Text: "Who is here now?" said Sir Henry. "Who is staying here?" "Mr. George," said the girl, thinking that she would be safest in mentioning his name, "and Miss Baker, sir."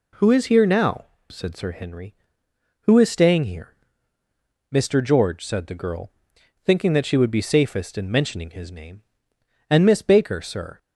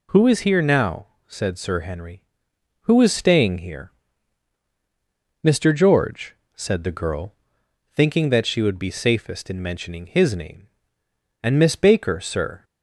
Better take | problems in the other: neither | none

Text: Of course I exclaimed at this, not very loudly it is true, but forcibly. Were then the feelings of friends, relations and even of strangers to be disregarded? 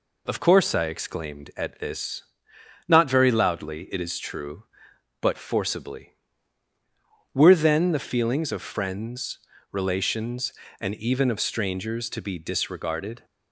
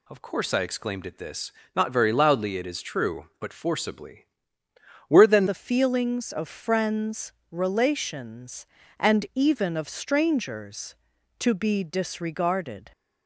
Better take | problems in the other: first | changes voice at "the"; from 5.4 s on; 7.5 s long

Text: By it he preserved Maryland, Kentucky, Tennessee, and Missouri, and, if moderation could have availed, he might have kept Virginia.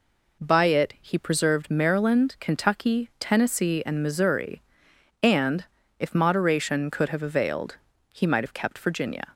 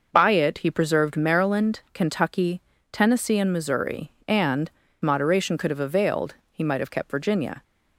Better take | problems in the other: first | skips "if"; at 4.8 s

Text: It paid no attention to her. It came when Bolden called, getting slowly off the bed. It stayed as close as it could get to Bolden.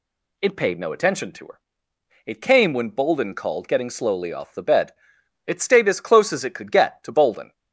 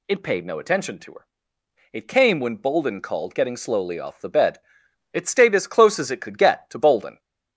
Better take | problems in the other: first | gets louder; slight; throughout; 2.5 dB

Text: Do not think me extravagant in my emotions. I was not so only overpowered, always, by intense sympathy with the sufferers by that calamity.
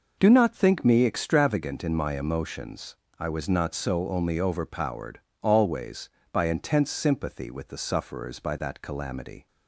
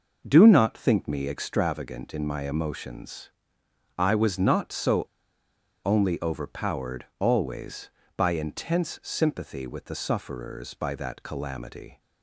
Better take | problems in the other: first | pauses between "so" and "only"; noticeable; at 5.0 s; 0.83 s long

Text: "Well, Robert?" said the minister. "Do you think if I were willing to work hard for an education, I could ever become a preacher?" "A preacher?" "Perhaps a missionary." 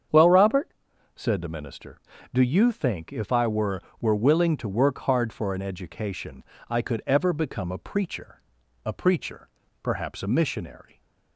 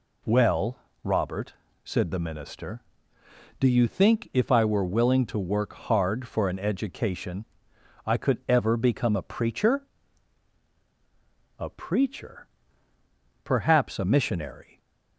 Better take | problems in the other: second | starts louder than the rest; strong; until 1.5 s; 7.5 dB // says "were" twice; at 4.0 s

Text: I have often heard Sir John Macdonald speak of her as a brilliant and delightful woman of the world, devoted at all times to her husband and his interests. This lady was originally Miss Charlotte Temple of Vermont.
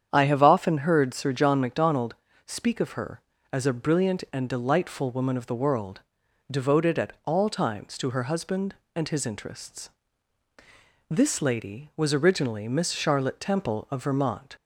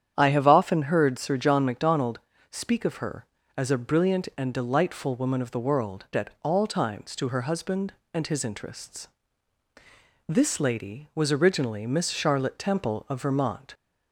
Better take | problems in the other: first | starts louder than the rest; strong; until 1.1 s; 9 dB; strong in the first // pauses between "Macdonald" and "speak"; slight; at 2.1 s; 0.32 s long; slight in the first // skips "devoted"; at 6.1 s

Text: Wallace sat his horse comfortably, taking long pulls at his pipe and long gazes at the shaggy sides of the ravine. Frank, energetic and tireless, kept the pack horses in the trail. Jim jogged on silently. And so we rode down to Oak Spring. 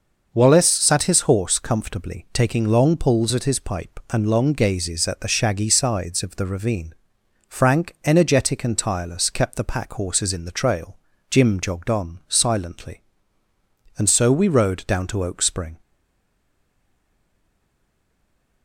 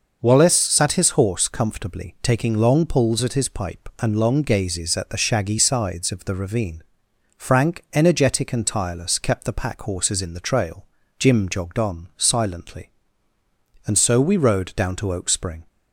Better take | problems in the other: second | starts louder than the rest; noticeable; until 1.3 s; 6 dB; noticeable in the second // stays silent after the last word; strong; from 15.8 s on; 2.8 s long

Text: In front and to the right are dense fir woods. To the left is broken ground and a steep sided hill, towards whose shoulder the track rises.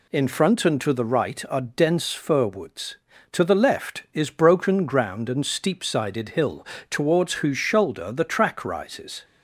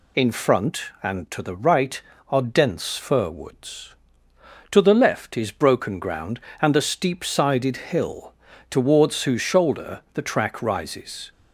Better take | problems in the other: second | skips "a"; at 5.4 s

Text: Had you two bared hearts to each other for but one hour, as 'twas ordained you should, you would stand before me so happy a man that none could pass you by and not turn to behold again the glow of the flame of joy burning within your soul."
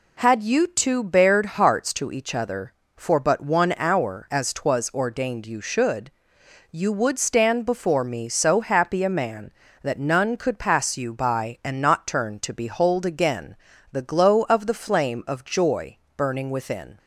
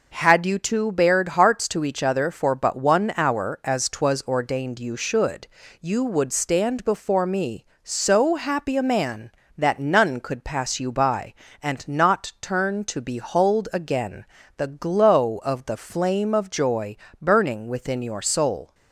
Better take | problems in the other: second | pauses between "again" and "the"; at 13.5 s; 0.38 s long; slight in the second // pauses between "joy" and "burning"; slight; at 15.9 s; 0.18 s long; slight in the second // stops before "your soul"; at 16.9 s

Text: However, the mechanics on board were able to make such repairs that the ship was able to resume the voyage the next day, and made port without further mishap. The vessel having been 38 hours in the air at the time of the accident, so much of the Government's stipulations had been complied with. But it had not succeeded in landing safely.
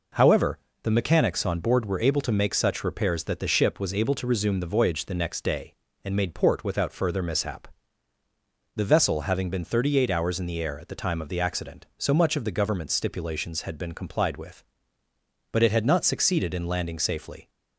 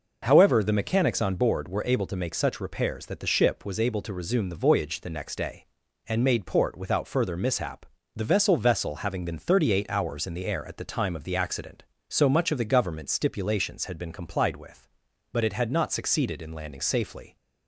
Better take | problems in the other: first | says "vessel" twice; at 8.5 s

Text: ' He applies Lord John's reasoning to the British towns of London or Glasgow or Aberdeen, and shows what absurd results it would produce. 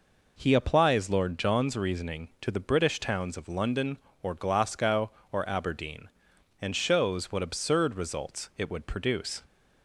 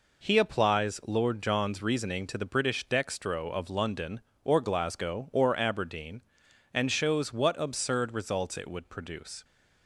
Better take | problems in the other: first | says "dextro" for "towns"; at 2.8 s

